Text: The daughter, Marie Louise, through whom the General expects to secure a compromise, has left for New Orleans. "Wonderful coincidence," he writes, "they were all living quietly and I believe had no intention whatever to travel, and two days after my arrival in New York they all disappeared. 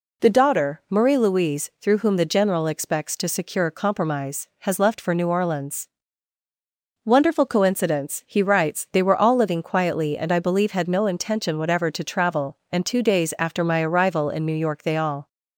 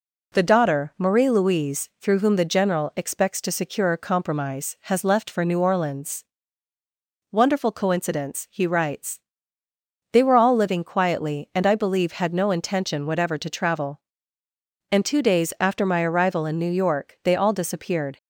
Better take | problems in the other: second | stops before "disappeared"; at 15.2 s

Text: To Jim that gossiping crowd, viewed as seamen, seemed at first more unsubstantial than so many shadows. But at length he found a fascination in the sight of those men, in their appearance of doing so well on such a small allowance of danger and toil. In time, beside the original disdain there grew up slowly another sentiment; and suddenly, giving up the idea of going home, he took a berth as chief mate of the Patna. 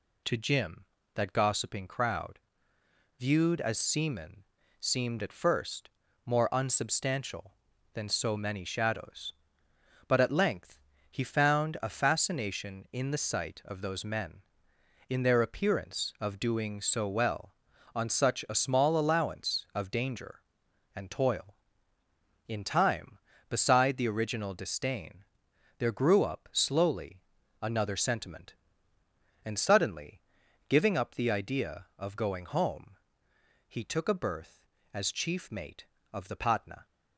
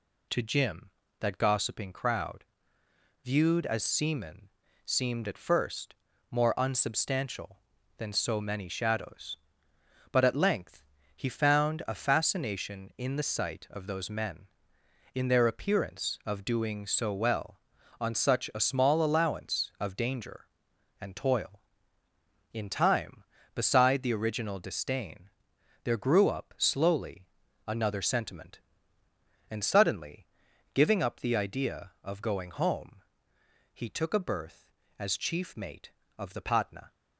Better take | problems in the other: neither | pauses between "first" and "more"; slight; the same in both // pauses between "length" and "he"; slight; the same in both // pauses between "disdain" and "there"; noticeable; the same in both // pauses between "slowly" and "another"; the same in both

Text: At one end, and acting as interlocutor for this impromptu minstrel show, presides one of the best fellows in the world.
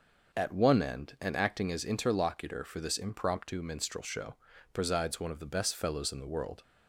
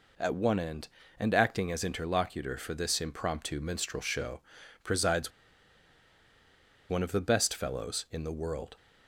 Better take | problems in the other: first | pauses between "presides" and "one"; strong; at 5.3 s; 1.5 s long

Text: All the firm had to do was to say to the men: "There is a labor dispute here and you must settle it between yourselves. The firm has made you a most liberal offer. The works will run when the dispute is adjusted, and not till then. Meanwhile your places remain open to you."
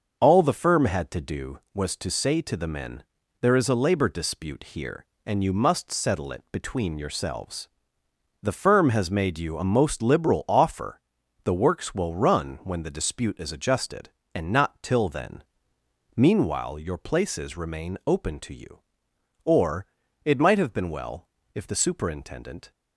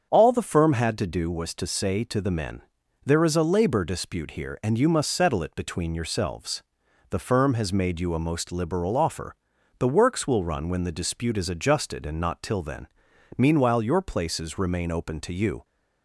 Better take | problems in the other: second | starts louder than the rest; until 1.2 s; 6 dB; strong in the second // goes on to say "Or it might have been well if the superintendent"; strong; from 19.4 s on; 3.2 s long

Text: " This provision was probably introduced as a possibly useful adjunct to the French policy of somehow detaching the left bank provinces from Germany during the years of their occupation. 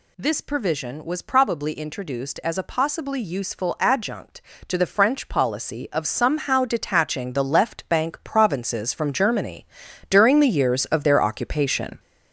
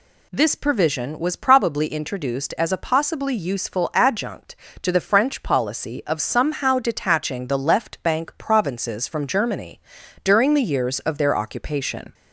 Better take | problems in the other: second | gets louder; noticeable; throughout; 6 dB // pauses between "Germany" and "during"; at 9.6 s; 0.42 s long; also in the second

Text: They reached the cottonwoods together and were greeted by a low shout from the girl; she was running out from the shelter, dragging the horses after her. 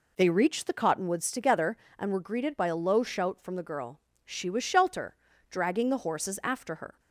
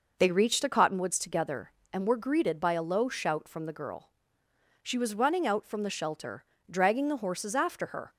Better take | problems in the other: second | skips "running out from the"; at 4.6 s

